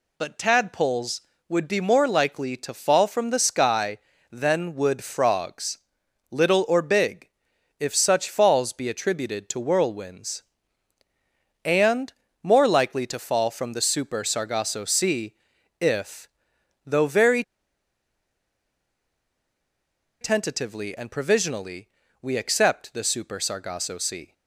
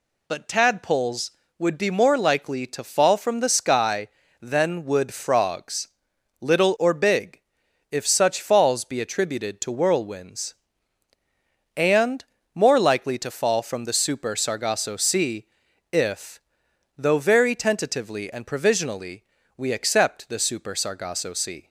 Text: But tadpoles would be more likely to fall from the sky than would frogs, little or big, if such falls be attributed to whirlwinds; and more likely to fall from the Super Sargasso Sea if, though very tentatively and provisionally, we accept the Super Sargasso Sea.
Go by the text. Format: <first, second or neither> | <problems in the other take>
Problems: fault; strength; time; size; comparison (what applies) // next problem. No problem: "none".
second | pauses between "and" and "more"; slight; at 12.1 s; 0.30 s long; slight in the second // pauses between "Sea" and "if"; noticeable; at 15.3 s; 0.46 s long; noticeable in the second // pauses between "very" and "tentatively"; strong; at 17.4 s; 2.7 s long